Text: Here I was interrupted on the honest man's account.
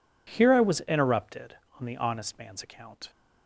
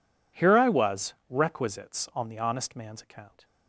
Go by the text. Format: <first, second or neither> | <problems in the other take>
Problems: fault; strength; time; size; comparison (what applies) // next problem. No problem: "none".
first | says "requisites" for "interrupted"; at 1.3 s